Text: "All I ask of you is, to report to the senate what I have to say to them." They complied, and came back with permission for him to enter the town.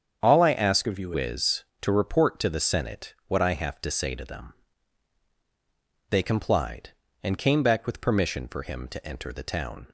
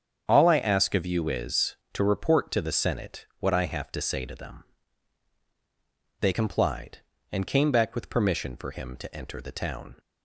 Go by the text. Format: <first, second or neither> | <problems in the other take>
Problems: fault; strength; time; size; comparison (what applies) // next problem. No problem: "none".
second | starts louder than the rest; strong; until 1.2 s; 7.5 dB; strong in the second // changes voice from "of" to "you"; from 0.8 to 1.1 s; 0.3 s long